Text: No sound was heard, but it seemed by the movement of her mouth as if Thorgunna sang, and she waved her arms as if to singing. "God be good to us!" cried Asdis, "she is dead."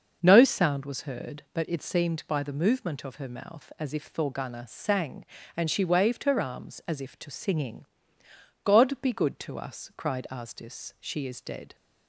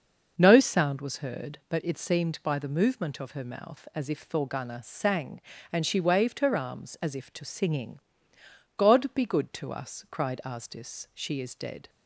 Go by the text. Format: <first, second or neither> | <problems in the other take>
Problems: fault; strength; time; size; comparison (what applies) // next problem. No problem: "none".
neither | starts louder than the rest; noticeable; the same in both